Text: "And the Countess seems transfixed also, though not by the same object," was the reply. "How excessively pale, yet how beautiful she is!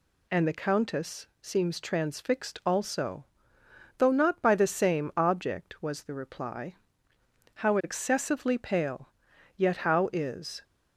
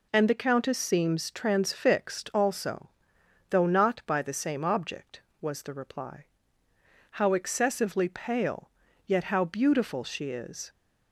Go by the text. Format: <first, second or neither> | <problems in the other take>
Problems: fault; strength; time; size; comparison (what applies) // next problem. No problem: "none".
second | skips "beautiful she"; at 10.1 s